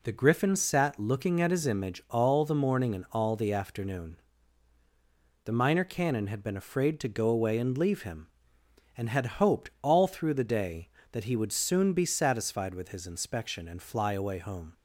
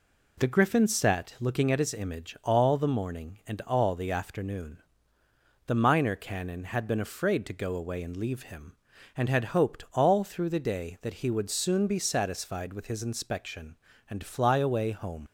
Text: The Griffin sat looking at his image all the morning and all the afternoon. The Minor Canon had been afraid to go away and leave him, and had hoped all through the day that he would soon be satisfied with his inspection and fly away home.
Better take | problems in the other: first | leaves "home" unfinished; at 15.2 s; 60 ms

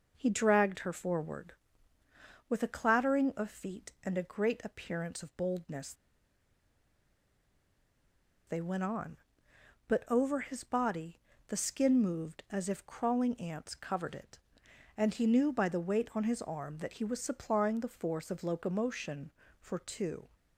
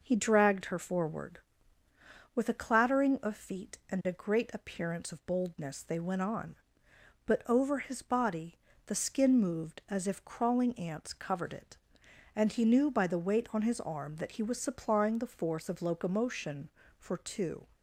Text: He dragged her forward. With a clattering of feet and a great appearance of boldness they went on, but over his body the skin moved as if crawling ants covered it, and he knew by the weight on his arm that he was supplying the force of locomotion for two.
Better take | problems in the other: second | pauses between "boldness" and "they"; strong; at 5.9 s; 2.5 s long // pauses between "body" and "the"; slight; at 11.2 s; 0.28 s long; slight in the second

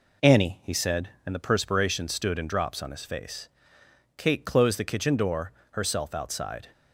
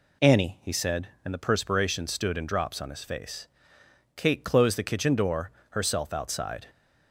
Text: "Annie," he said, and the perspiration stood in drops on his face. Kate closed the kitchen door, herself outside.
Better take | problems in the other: second | gets quieter; slight; throughout; 3 dB

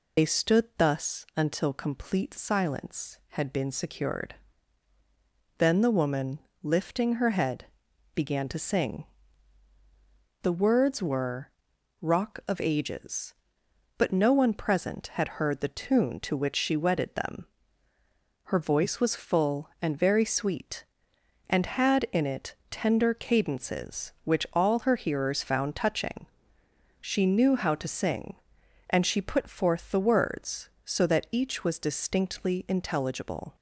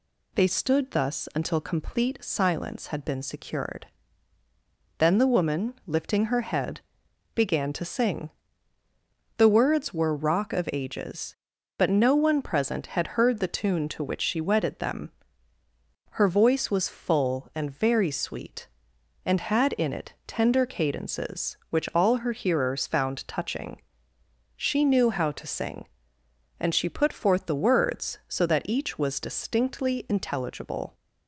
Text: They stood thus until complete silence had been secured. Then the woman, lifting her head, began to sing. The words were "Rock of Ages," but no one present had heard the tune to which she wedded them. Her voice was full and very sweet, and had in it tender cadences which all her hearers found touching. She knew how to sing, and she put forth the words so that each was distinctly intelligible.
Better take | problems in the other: second | loses the start of "They"; at 0.1 s; 75 ms // pauses between "were" and "Rock"; noticeable; at 11.4 s; 0.52 s long

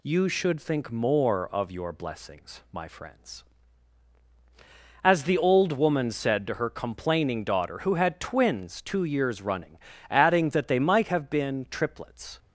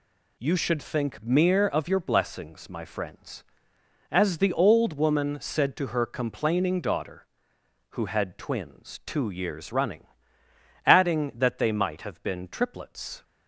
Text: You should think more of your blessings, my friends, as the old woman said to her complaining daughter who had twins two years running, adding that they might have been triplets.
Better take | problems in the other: first | says "mere" for "more"; at 1.2 s

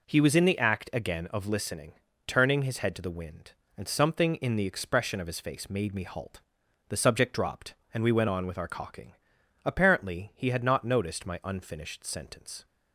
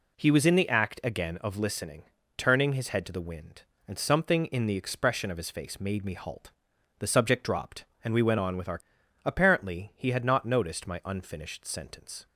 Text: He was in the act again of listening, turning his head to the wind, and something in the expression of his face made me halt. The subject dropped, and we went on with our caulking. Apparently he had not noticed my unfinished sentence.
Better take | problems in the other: first | skips "caulking"; at 9.0 s

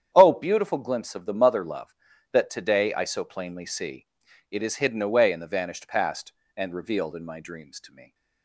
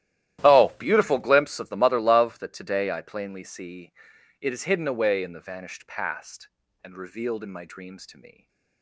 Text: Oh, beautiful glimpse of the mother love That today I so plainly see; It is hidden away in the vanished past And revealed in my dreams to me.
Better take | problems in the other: first | starts louder than the rest; strong; until 1.4 s; 13.5 dB; strong in the first // skips "so"; at 3.0 s // stays silent after the last word; slight; from 8.3 s on; 0.5 s long

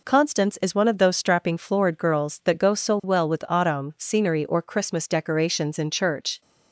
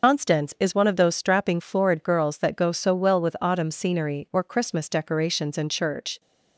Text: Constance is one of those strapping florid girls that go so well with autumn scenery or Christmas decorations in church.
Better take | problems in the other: first | loses the start of "Constance"; at 0.0 s; 100 ms

